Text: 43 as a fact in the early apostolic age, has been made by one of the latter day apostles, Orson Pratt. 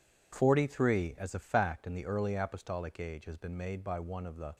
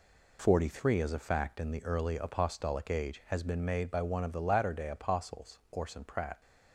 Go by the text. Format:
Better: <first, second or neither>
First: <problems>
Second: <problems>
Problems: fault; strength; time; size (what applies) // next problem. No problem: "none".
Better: second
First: stops before "latter day apostles Orson Pratt"; at 4.5 s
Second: none